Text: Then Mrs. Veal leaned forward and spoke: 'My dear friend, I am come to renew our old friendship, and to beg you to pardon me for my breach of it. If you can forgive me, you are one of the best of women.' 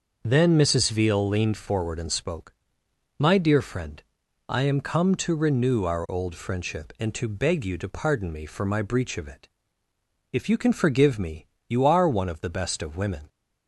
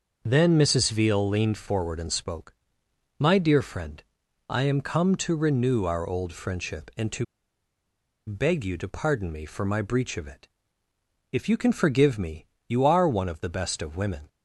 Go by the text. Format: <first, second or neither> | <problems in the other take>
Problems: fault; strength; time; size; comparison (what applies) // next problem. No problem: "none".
first | starts louder than the rest; until 1.2 s; 6.5 dB; also in the first // pauses between "to" and "beg"; at 7.2 s; 1.0 s long